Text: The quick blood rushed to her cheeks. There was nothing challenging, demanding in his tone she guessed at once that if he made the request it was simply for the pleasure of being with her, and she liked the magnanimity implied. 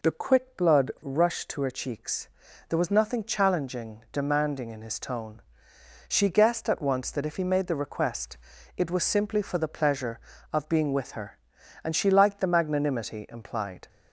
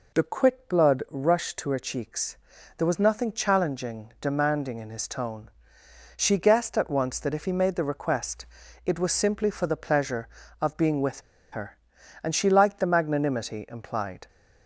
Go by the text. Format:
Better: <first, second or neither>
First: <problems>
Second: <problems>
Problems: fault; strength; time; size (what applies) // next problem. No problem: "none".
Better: first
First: pauses between "tone" and "she"; noticeable; at 5.4 s; 0.66 s long // pauses between "request" and "it"; at 8.3 s; 0.40 s long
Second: pauses between "tone" and "she"; noticeable; at 5.5 s; 0.66 s long // pauses between "request" and "it"; at 8.4 s; 0.40 s long // pauses between "with" and "her"; slight; at 11.2 s; 0.31 s long